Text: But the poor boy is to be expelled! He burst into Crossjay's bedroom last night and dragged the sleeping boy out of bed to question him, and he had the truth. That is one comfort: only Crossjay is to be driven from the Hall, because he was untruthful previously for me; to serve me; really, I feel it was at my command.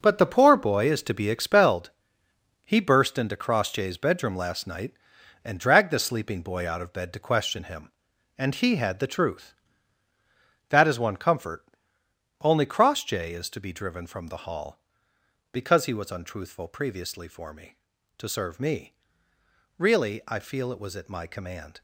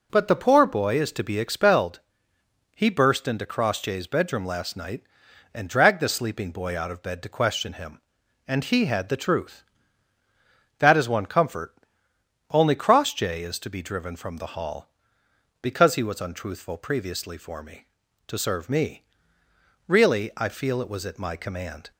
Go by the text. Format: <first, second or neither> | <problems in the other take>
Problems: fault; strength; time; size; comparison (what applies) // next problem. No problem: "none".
second | gets quieter; strong; throughout; 10.5 dB